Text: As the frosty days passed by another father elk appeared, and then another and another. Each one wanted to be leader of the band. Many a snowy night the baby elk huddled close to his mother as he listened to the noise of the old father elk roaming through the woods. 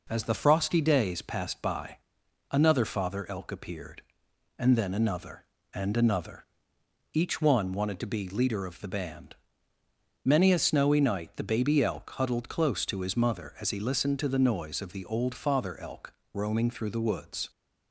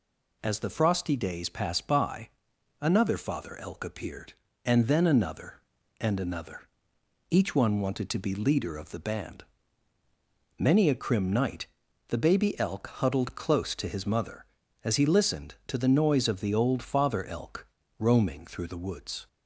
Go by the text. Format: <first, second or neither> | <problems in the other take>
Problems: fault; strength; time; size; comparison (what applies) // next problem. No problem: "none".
first | pauses between "by" and "another"; noticeable; at 2.2 s; 0.50 s long; noticeable in the first // says "crim" for "snowy"; at 10.9 s // pauses between "night" and "the"; at 11.6 s; 0.42 s long // pauses between "elk" and "roaming"; slight; at 17.6 s; 0.32 s long; slight in the first